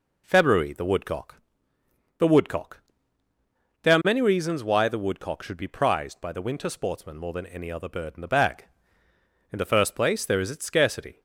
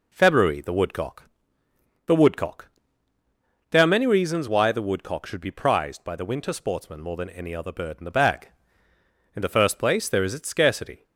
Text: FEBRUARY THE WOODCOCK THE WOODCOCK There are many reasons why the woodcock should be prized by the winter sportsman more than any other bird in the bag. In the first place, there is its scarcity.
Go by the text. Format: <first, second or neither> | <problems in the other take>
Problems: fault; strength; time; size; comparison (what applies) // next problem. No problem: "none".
neither | pauses between "WOODCOCK" and "THE"; noticeable; the same in both // pauses between "WOODCOCK" and "There"; the same in both